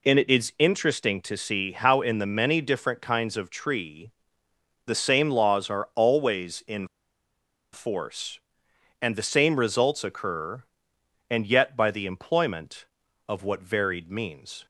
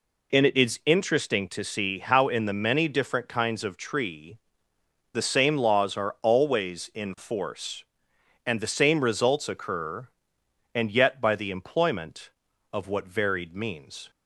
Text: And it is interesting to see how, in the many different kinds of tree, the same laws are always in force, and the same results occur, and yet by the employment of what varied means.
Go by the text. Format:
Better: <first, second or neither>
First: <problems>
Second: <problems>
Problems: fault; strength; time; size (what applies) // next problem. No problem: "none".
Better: second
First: pauses between "in" and "force"; noticeable; at 6.8 s; 0.87 s long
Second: none